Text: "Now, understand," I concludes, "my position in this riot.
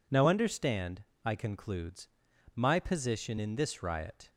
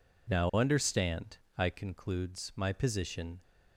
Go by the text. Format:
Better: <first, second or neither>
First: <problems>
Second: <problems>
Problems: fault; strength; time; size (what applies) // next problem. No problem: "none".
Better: first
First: none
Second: stops before "in this riot"; at 3.4 s